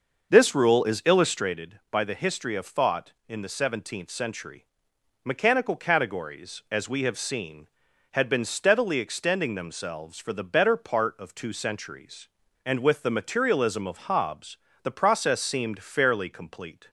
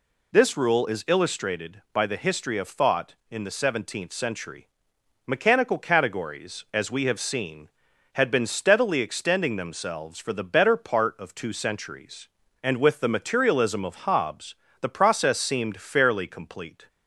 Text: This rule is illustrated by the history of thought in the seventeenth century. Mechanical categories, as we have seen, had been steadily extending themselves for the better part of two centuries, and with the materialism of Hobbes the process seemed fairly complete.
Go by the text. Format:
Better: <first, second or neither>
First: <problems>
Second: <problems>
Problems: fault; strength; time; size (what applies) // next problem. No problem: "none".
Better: second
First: starts louder than the rest; noticeable; until 1.7 s; 6 dB // pauses between "Hobbes" and "the"; slight; at 14.5 s; 0.26 s long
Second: pauses between "Hobbes" and "the"; slight; at 14.5 s; 0.26 s long